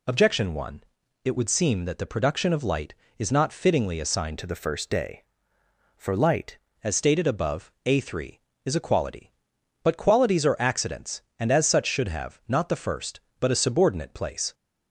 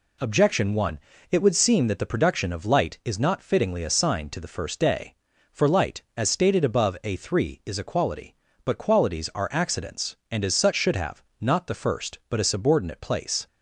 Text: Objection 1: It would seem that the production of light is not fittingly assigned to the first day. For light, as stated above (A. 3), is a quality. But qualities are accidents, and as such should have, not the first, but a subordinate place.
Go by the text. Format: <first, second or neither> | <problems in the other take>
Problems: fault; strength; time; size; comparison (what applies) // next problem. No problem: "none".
second | changes voice from "to" to "light"; from 4.3 to 6.5 s; 2.2 s long